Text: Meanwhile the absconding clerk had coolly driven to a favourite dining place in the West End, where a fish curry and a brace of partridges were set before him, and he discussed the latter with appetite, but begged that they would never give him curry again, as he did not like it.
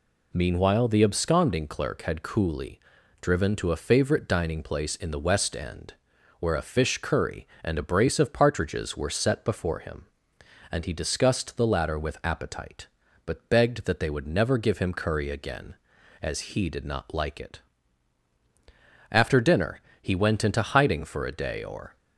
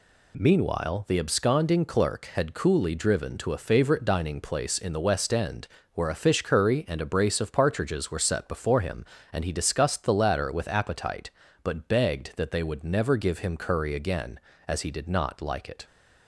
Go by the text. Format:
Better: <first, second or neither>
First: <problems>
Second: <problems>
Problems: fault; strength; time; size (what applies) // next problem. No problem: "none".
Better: second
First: pauses between "coolly" and "driven"; at 2.7 s; 0.42 s long // goes on to say "After dinner he went into hiding for a day or"; strong; from 19.1 s on; 2.8 s long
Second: none